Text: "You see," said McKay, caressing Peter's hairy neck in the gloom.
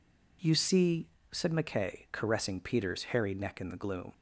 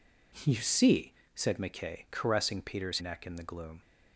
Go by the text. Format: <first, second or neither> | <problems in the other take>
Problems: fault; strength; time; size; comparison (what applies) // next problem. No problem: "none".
first | skips "hairy"; at 3.0 s